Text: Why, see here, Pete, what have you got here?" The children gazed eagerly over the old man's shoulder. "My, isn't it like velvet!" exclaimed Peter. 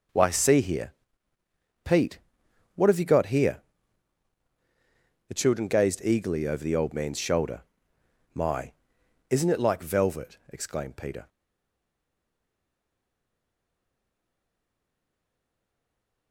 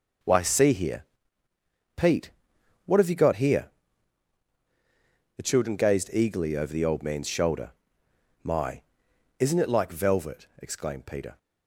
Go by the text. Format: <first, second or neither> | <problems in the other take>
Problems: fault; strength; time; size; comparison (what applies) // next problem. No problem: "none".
second | stays silent after the last word; strong; from 11.2 s on; 5.1 s long